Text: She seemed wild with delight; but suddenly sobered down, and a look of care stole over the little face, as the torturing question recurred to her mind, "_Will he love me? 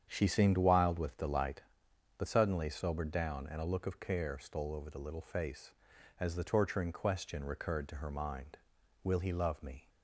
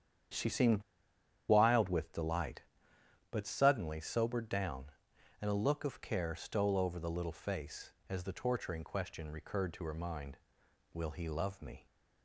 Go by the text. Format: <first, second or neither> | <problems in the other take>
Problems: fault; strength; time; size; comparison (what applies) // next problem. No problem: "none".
first | starts louder than the rest; strong; until 2.0 s; 9 dB; strong in the first // pauses between "seemed" and "wild"; noticeable; at 0.8 s; 0.68 s long